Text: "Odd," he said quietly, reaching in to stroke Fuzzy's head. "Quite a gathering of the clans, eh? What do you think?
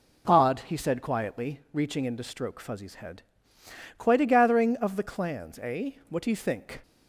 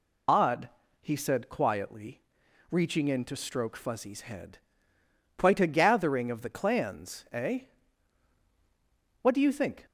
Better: first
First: none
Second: loses the start of "Odd"; at 0.2 s; 70 ms

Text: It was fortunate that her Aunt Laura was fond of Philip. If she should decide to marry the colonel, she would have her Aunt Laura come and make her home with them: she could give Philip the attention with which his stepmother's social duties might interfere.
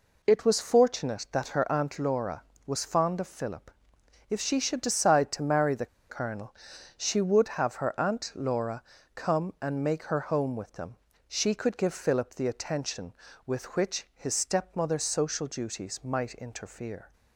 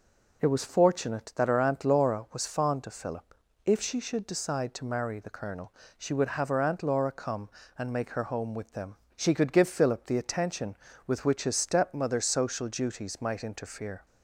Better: second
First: pauses between "the" and "colonel"; slight; at 5.8 s; 0.22 s long // pauses between "Laura" and "come"; slight; at 8.8 s; 0.32 s long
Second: none

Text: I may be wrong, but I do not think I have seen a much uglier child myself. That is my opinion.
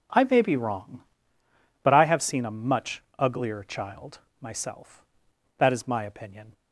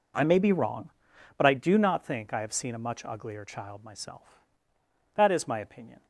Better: second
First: skips "do not think I"; at 2.0 s // pauses between "much" and "uglier"; slight; at 3.0 s; 0.16 s long // pauses between "child" and "myself"; slight; at 4.1 s; 0.22 s long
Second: none

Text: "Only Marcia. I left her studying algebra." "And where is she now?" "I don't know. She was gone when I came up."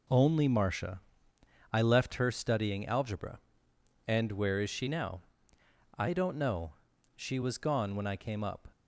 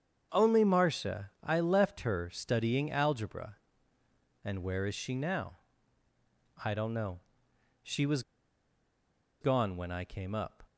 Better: first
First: none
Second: starts louder than the rest; strong; until 1.3 s; 7.5 dB // pauses between "was" and "gone"; at 8.2 s; 1.1 s long

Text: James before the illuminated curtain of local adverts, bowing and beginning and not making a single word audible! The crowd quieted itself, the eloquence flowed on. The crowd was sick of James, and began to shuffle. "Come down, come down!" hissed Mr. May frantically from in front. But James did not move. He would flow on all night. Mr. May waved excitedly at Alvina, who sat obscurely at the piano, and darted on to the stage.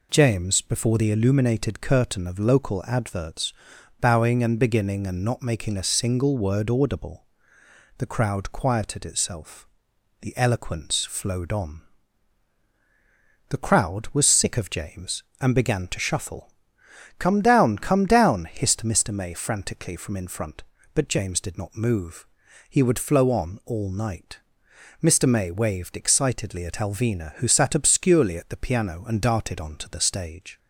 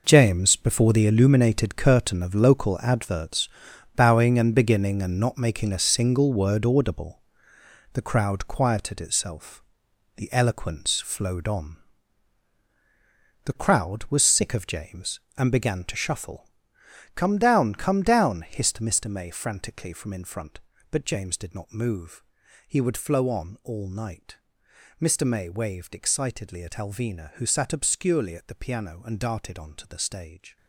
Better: first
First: none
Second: gets quieter; strong; throughout; 12.5 dB

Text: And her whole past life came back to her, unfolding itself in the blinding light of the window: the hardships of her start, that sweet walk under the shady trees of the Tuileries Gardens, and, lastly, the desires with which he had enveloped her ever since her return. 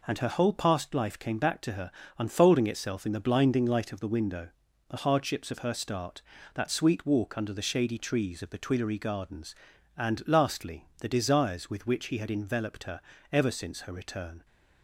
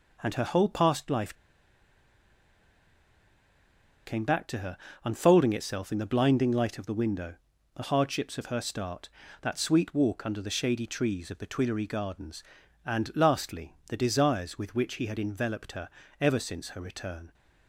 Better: first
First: pauses between "her" and "ever"; slight; at 13.0 s; 0.32 s long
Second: pauses between "life" and "came"; strong; at 1.3 s; 2.7 s long // pauses between "her" and "ever"; slight; at 15.8 s; 0.32 s long

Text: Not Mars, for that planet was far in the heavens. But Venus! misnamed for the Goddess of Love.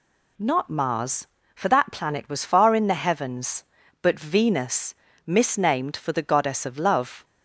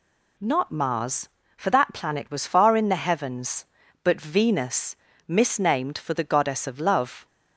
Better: neither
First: none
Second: none

